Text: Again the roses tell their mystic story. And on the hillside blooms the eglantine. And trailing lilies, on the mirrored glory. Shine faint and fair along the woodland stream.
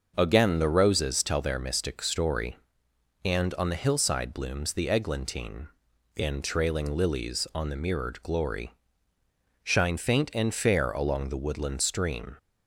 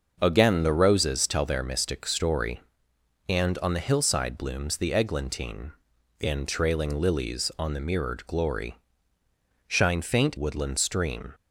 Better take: first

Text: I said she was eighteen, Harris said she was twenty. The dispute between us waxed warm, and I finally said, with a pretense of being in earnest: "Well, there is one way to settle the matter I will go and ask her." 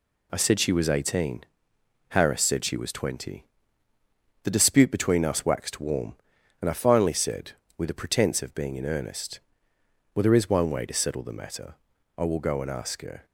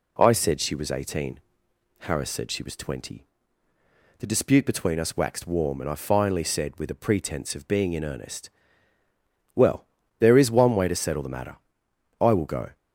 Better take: first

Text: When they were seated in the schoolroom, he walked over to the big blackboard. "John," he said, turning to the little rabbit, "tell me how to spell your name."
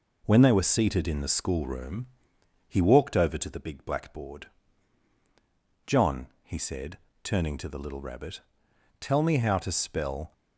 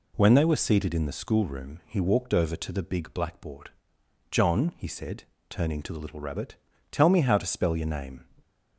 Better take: second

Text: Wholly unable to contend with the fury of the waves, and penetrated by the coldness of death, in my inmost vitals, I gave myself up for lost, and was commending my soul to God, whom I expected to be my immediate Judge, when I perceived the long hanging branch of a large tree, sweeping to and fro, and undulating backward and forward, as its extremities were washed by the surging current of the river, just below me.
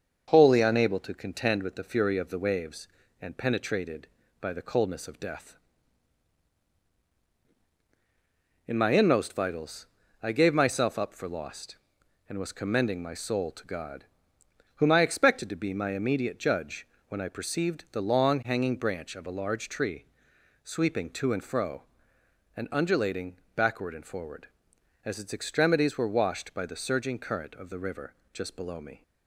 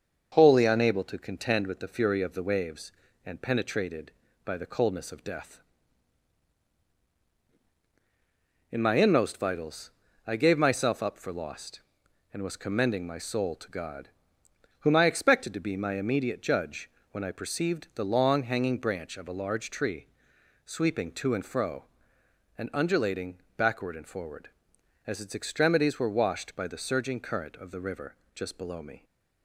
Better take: neither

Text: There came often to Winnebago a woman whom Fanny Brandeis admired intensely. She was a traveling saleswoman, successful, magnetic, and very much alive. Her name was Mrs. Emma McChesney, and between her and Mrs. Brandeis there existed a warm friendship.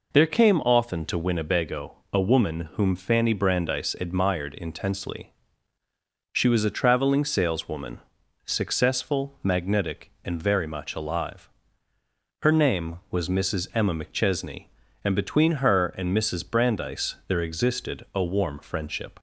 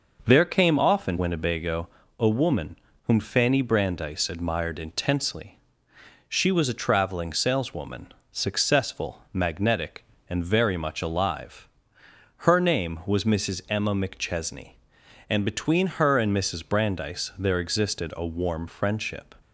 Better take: first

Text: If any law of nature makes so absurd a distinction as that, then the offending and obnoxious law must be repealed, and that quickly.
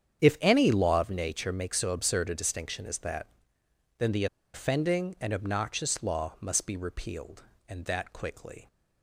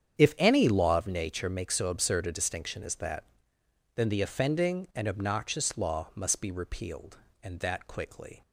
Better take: second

